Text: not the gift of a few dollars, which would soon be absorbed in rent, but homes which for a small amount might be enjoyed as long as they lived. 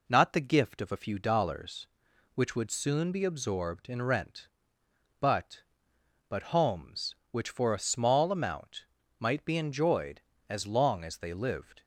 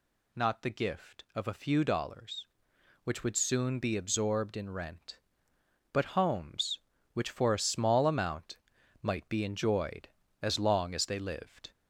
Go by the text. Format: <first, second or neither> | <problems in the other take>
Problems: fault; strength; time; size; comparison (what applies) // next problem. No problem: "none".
second | says "but" twice; at 6.2 s // pauses between "amount" and "might"; slight; at 8.8 s; 0.36 s long; noticeable in the second